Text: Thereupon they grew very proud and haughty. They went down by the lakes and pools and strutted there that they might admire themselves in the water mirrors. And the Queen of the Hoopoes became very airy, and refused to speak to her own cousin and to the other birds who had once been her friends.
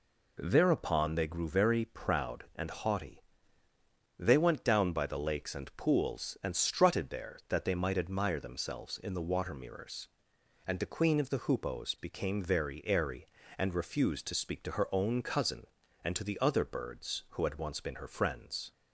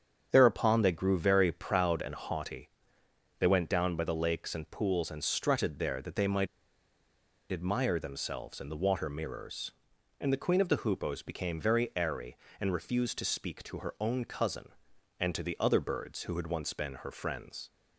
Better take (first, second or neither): first